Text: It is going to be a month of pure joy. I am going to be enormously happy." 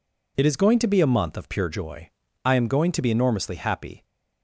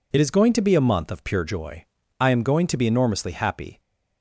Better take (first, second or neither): neither